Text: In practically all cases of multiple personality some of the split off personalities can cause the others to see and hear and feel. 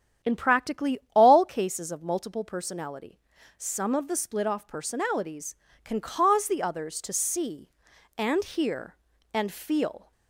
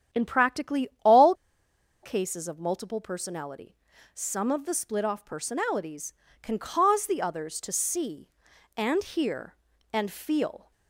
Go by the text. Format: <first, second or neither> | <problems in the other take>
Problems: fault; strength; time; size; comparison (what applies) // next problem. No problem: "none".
first | starts louder than the rest; strong; until 1.3 s; 9.5 dB; strong in the first // pauses between "practically" and "all"; slight; at 0.8 s; 0.16 s long; slight in the first // pauses between "all" and "cases"; noticeable; at 1.3 s; 0.69 s long // pauses between "personality" and "some"; at 3.7 s; 0.40 s long; also in the first